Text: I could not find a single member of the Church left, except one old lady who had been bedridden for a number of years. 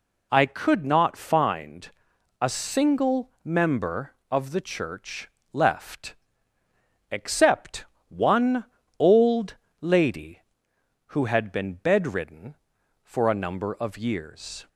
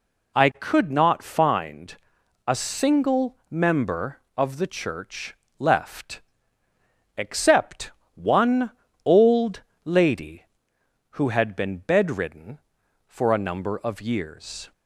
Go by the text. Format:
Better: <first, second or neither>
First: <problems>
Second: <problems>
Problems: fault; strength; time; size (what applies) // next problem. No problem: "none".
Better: neither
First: pauses between "find" and "a"; noticeable; at 1.8 s; 0.52 s long // pauses between "single" and "member"; slight; at 3.2 s; 0.16 s long // pauses between "Church" and "left"; slight; at 5.2 s; 0.24 s long // pauses between "except" and "one"; slight; at 7.8 s; 0.24 s long // pauses between "one" and "old"; slight; at 8.6 s; 0.34 s long // pauses between "old" and "lady"; slight; at 9.5 s; 0.26 s long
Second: pauses between "find" and "a"; noticeable; at 1.9 s; 0.52 s long // pauses between "single" and "member"; slight; at 3.3 s; 0.16 s long // pauses between "Church" and "left"; slight; at 5.3 s; 0.24 s long // pauses between "except" and "one"; slight; at 7.9 s; 0.24 s long // pauses between "one" and "old"; slight; at 8.7 s; 0.34 s long // pauses between "old" and "lady"; slight; at 9.6 s; 0.24 s long